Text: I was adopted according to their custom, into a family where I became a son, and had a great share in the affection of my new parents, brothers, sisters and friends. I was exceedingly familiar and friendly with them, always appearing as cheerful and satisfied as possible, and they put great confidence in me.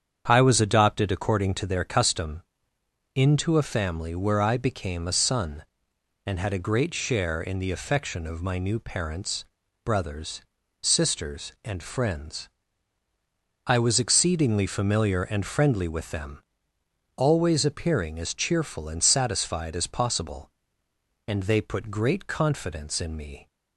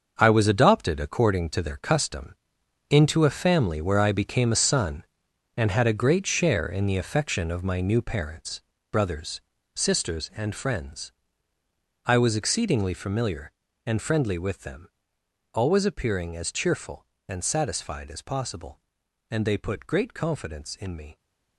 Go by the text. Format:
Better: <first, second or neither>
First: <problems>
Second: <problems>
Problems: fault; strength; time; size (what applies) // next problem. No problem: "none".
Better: first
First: starts louder than the rest; strong; until 1.2 s; 8 dB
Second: gets quieter; strong; throughout; 10.5 dB // starts louder than the rest; until 1.2 s; 6.5 dB